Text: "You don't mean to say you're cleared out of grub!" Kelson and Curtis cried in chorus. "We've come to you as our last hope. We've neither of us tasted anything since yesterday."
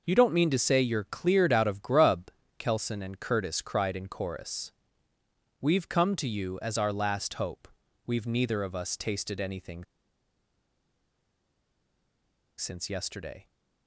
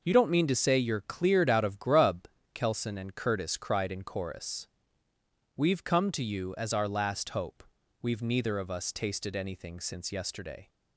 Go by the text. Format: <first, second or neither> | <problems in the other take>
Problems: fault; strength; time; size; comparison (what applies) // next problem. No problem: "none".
second | pauses between "anything" and "since"; strong; at 9.8 s; 2.7 s long